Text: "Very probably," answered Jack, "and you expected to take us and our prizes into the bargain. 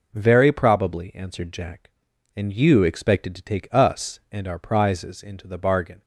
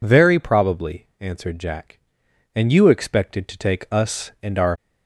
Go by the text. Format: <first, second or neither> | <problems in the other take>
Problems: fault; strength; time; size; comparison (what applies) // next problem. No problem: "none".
first | stops before "prizes into the bargain"; at 4.7 s